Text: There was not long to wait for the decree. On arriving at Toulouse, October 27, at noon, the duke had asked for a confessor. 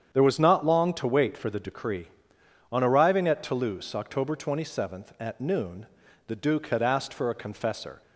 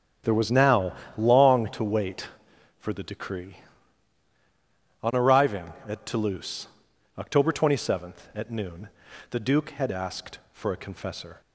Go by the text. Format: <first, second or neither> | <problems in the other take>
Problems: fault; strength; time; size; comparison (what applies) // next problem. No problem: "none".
first | starts louder than the rest; strong; until 1.5 s; 10.5 dB; strong in the first // says "now" for "not"; at 0.5 s